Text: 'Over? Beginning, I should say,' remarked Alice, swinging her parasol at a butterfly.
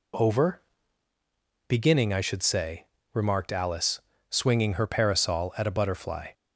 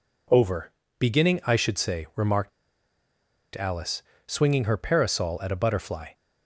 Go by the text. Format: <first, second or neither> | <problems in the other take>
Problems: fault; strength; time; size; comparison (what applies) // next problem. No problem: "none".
first | pauses between "remarked" and "Alice"; at 2.5 s; 1.0 s long